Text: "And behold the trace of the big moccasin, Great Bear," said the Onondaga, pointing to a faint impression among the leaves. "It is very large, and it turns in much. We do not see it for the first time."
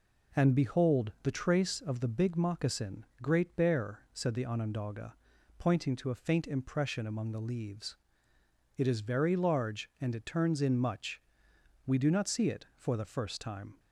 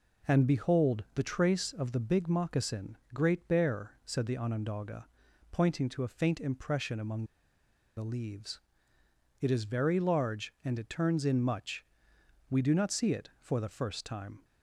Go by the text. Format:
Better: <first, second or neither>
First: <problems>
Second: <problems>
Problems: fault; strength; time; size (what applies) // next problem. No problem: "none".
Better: first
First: none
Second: pauses between "among" and "the"; noticeable; at 7.2 s; 0.71 s long